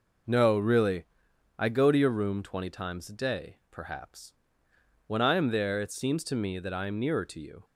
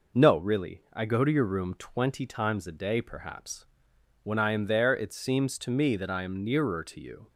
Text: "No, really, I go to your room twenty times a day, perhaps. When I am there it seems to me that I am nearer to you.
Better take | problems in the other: neither | none

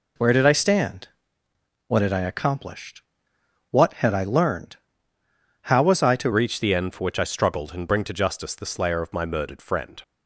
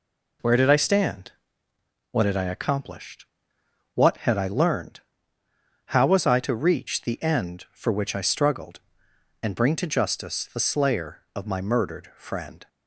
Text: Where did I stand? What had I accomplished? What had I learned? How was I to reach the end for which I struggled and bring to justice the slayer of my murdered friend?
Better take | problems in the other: second | changes voice at "reach"; from 6.3 s on; 3.7 s long

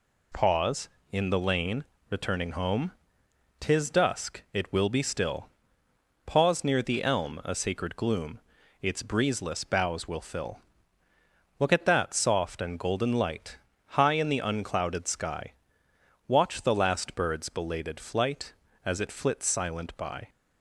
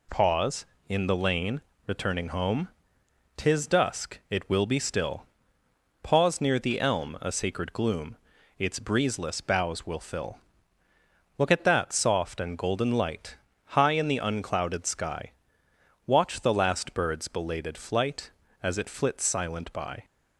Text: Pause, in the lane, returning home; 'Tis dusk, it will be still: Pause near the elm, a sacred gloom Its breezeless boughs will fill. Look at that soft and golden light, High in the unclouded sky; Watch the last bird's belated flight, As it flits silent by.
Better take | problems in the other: neither | pauses between "gloom" and "Its"; the same in both

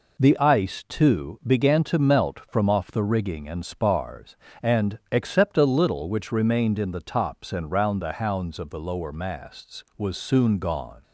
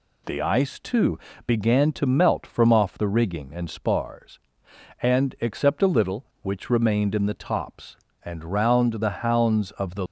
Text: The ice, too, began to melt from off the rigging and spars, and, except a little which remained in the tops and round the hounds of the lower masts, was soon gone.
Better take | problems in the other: first | stops before "lower masts was soon gone"; at 10.0 s

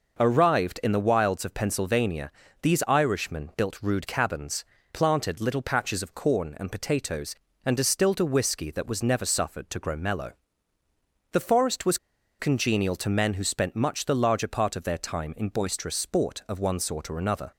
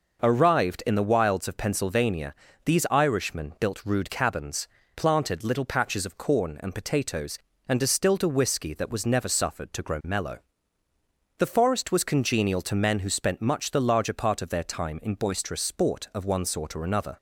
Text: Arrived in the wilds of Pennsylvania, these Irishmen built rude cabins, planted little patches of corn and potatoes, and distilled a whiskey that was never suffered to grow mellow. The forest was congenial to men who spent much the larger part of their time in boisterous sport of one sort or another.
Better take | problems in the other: second | pauses between "was" and "congenial"; at 11.9 s; 0.41 s long

